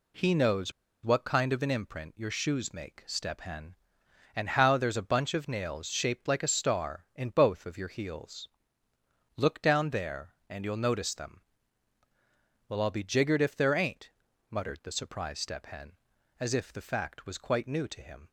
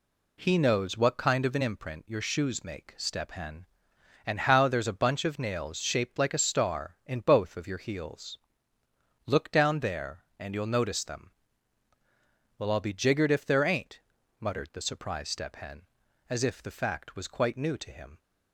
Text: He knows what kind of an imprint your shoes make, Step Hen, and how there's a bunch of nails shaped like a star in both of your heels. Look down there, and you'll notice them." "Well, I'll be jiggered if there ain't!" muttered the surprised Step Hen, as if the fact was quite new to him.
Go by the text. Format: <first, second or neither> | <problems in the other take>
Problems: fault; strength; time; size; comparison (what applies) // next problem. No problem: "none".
second | pauses between "knows" and "what"; slight; at 0.7 s; 0.32 s long